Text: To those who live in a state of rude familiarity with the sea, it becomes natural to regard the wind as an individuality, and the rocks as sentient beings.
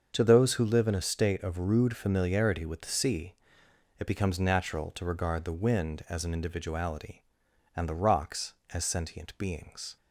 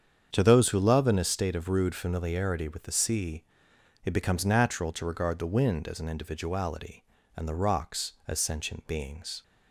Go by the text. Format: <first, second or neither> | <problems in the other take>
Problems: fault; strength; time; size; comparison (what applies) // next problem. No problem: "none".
first | starts louder than the rest; strong; until 1.3 s; 7.5 dB; also in the first // says "love" for "live"; at 0.7 s